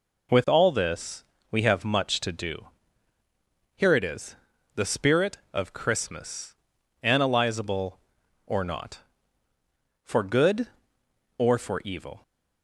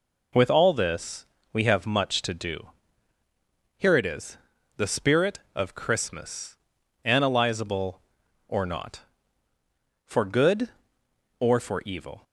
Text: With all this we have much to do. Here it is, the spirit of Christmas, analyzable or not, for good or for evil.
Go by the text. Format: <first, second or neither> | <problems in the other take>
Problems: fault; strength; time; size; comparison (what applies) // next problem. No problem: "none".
neither | pauses between "this" and "we"; slight; the same in both